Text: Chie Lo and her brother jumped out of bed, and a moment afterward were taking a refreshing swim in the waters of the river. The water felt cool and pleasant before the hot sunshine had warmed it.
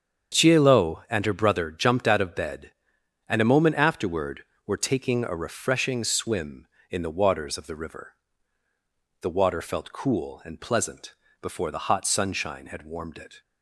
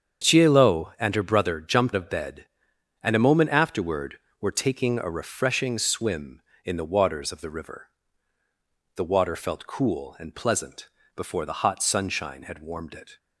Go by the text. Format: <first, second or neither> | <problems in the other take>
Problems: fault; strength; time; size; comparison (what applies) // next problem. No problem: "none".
first | starts louder than the rest; strong; until 1.3 s; 7.5 dB; strong in the first // skips "out"; at 1.9 s // pauses between "pleasant" and "before"; slight; at 10.8 s; 0.30 s long; slight in the first